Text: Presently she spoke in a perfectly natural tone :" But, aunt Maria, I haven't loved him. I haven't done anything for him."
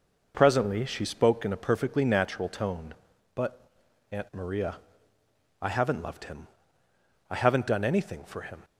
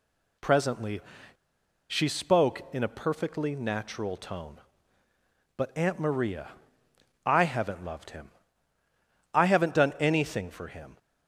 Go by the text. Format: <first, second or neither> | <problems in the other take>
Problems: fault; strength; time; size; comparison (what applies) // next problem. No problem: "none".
first | pauses between "Presently" and "she"; noticeable; at 1.0 s; 0.89 s long